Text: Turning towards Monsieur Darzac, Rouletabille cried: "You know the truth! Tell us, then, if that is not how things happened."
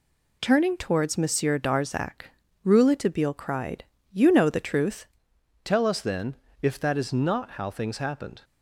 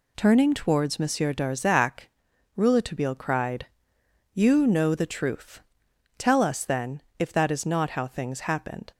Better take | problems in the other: second | changes voice at "Tell"; from 5.6 s on; 2.8 s long

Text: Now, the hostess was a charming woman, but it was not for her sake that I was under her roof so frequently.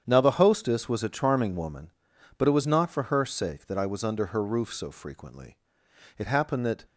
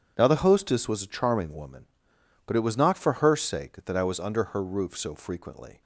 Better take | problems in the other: second | starts louder than the rest; strong; until 1.0 s; 8.5 dB // goes on to say "It happened that"; noticeable; from 6.1 s on; 0.66 s long

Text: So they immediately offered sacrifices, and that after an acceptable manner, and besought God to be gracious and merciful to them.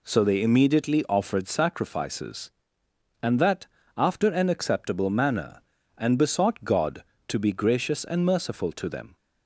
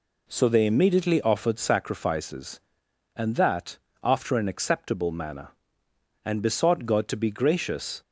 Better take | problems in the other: first | pauses between "that" and "after"; slight; at 3.7 s; 0.26 s long; slight in the first // stops before "and merciful to them"; at 8.0 s

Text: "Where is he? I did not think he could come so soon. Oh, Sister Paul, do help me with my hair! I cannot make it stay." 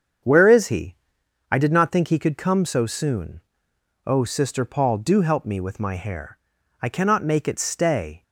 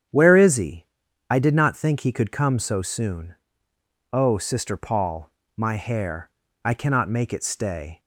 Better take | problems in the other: first | starts louder than the rest; strong; until 1.5 s; 8.5 dB; strong in the first // skips "do help me with"; at 5.4 s

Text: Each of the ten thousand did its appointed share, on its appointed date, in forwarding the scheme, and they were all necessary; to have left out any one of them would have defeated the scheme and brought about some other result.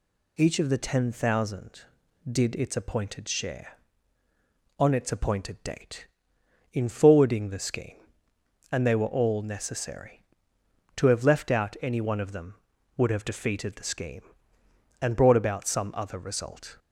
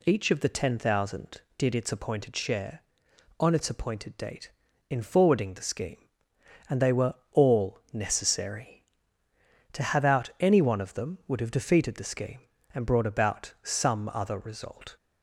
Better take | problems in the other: first | pauses between "were" and "all"; slight; at 7.1 s; 0.18 s long // skips "left"; at 10.0 s

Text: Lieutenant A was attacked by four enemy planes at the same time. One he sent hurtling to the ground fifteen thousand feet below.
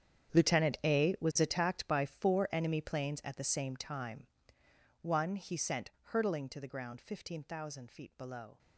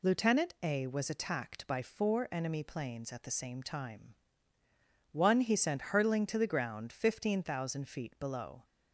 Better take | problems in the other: second | gets quieter; strong; throughout; 16.5 dB // pauses between "sent" and "hurtling"; slight; at 5.9 s; 0.20 s long

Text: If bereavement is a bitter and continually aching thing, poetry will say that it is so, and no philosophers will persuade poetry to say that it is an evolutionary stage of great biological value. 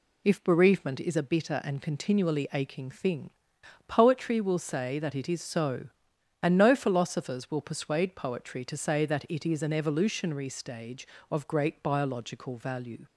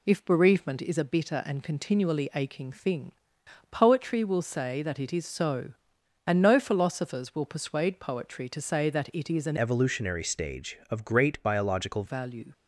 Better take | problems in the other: first | changes voice from "evolutionary" to "biological"; from 9.5 to 12.0 s; 2.5 s long

